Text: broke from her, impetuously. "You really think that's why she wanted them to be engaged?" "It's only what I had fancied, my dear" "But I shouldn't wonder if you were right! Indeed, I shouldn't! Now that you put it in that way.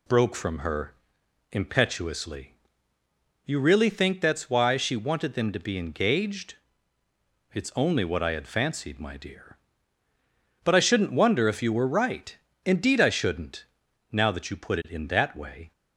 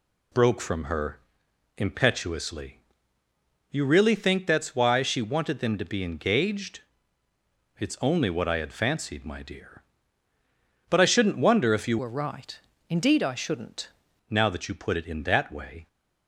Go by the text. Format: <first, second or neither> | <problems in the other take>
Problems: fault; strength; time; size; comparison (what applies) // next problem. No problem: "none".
first | changes voice from "were" to "shouldn't"; from 11.9 to 13.8 s; 1.9 s long